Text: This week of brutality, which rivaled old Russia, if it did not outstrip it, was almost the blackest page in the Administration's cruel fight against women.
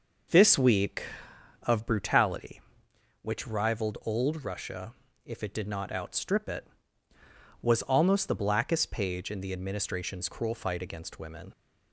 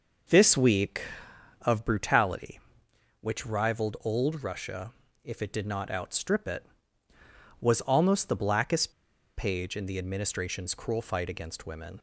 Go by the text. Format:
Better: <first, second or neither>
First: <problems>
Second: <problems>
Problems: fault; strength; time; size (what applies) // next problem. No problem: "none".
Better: first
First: none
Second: pauses between "blackest" and "page"; noticeable; at 8.8 s; 0.47 s long